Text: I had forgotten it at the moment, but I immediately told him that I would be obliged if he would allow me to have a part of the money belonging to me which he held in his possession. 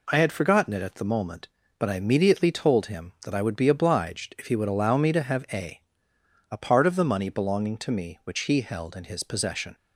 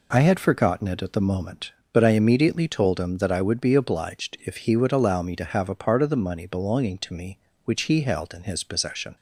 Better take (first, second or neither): second